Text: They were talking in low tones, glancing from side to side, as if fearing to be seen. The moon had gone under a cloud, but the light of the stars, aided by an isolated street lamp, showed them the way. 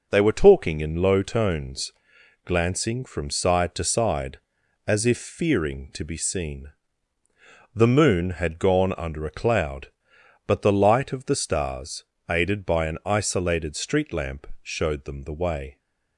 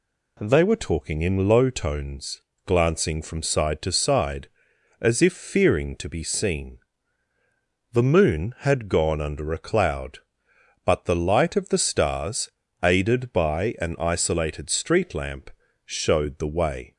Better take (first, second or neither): first